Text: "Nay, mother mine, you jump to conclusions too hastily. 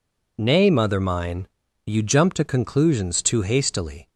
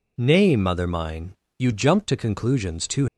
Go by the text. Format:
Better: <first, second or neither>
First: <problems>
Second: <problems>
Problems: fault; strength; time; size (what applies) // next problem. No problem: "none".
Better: first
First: none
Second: stops before "hastily"; at 3.0 s